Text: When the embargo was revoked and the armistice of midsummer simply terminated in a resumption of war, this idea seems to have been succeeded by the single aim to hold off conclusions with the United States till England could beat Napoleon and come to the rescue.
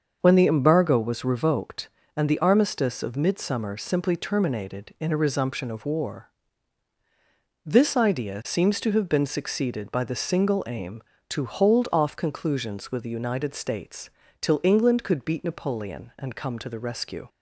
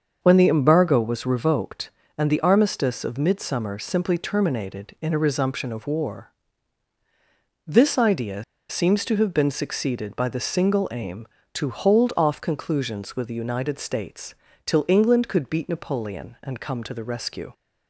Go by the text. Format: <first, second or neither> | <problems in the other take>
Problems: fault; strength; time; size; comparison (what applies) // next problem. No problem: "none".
first | starts louder than the rest; until 1.2 s; 6.5 dB; also in the first // pauses between "idea" and "seems"; slight; at 8.4 s; 0.25 s long // pauses between "States" and "till"; slight; at 14.3 s; 0.30 s long; slight in the first